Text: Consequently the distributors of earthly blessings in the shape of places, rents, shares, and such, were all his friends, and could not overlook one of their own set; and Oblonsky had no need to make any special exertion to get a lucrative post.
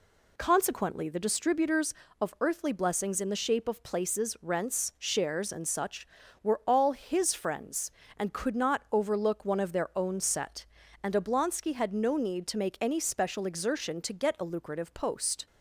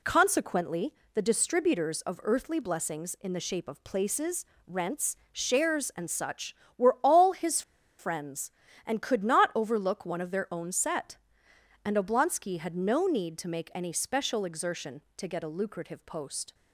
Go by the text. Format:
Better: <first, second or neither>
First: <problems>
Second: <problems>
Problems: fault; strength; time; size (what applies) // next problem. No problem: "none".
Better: first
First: none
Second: pauses between "Consequently" and "the"; slight; at 0.9 s; 0.20 s long // pauses between "his" and "friends"; at 7.6 s; 0.37 s long